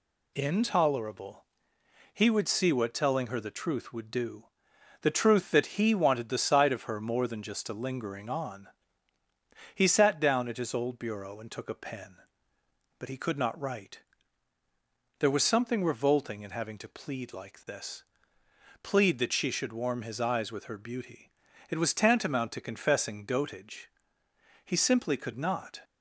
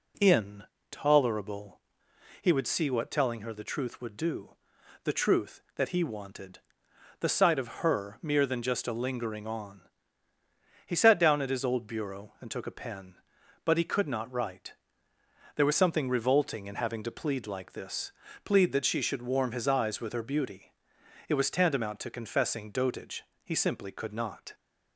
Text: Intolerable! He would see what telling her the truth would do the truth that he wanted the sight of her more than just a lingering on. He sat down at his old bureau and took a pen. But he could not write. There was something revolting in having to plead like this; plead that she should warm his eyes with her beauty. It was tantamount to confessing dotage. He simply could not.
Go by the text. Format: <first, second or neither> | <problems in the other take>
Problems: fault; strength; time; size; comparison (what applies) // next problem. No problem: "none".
first | pauses between "do" and "the"; noticeable; at 4.5 s; 0.52 s long; noticeable in the first // pauses between "wanted" and "the"; noticeable; at 6.5 s; 0.60 s long // says "mere" for "more"; at 8.2 s